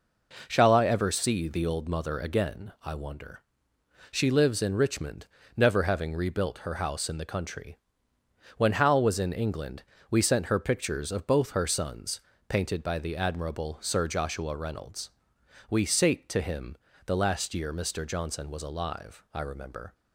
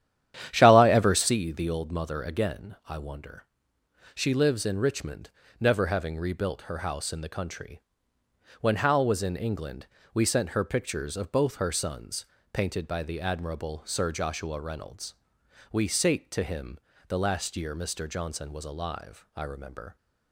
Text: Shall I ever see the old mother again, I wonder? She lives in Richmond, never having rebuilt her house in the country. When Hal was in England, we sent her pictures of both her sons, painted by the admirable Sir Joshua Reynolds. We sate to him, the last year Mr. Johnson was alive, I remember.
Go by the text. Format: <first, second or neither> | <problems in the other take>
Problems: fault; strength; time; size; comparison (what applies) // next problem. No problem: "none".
first | starts louder than the rest; strong; until 1.4 s; 10.5 dB